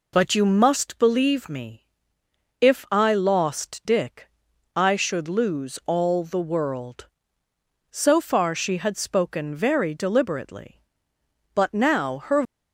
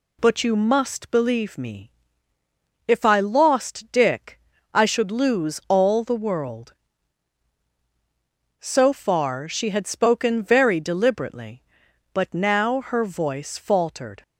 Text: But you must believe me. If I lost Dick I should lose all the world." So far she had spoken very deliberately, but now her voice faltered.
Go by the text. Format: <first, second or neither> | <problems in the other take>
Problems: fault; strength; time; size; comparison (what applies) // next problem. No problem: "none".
second | pauses between "Dick" and "I"; noticeable; at 4.2 s; 0.48 s long; slight in the second // stops before "voice faltered"; at 12.4 s